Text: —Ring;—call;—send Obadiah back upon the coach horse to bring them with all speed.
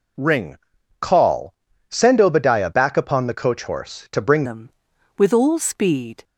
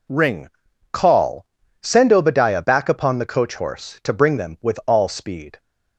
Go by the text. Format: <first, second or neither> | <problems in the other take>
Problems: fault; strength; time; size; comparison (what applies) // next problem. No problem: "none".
second | changes voice at "them"; from 4.4 s on; 1.8 s long